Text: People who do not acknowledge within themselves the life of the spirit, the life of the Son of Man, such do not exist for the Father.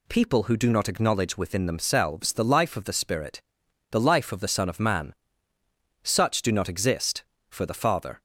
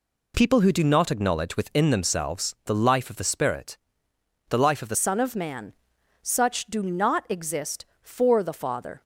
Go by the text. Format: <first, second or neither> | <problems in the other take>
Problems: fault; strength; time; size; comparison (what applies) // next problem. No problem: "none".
first | changes voice at "Son"; from 4.9 s on; 4.1 s long